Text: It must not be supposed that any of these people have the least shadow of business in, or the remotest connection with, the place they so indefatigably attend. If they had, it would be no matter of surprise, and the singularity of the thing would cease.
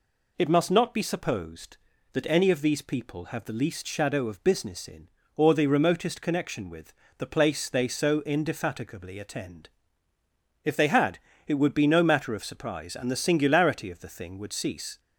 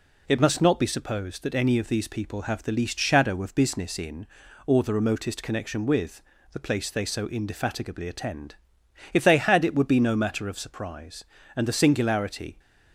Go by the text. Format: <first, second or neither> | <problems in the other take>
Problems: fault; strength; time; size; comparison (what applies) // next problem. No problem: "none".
first | stops before "of the thing would cease"; at 12.5 s